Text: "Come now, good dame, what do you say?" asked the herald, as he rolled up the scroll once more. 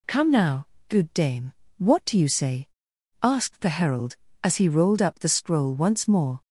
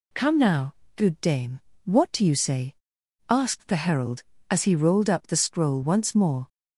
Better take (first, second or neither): neither